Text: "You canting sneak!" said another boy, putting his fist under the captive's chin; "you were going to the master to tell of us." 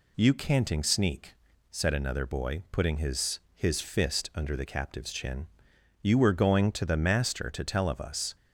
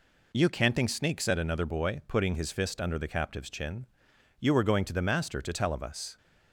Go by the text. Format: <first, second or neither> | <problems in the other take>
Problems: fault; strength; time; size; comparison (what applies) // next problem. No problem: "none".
second | says "his" twice; at 3.5 s